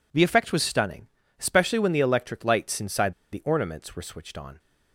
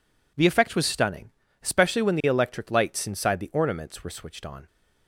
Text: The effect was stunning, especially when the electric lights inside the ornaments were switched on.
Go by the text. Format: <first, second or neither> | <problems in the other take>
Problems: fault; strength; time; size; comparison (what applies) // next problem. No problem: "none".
second | pauses between "inside" and "the"; slight; at 3.1 s; 0.18 s long